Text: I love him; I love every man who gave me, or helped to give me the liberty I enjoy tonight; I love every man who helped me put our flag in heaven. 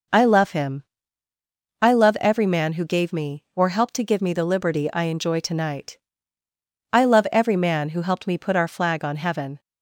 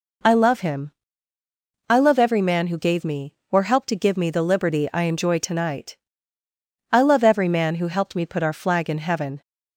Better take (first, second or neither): second